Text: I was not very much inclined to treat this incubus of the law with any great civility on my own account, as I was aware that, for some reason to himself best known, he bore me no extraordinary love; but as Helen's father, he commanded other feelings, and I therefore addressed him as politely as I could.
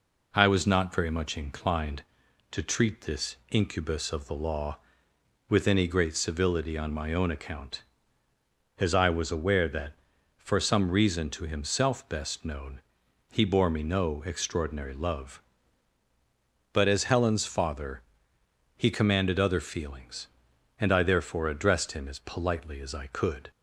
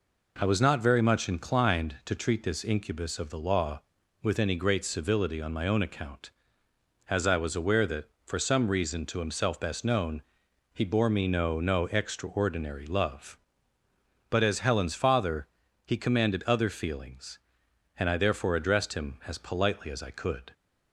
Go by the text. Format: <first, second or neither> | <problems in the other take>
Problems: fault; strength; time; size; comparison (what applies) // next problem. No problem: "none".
first | says "no" twice; at 11.6 s